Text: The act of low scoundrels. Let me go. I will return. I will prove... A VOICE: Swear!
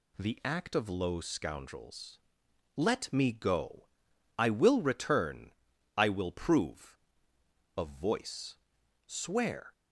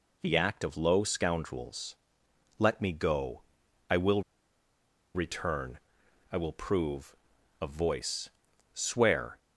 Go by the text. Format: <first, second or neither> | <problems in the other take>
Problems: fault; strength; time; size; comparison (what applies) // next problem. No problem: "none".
first | pauses between "will" and "return"; noticeable; at 4.2 s; 0.94 s long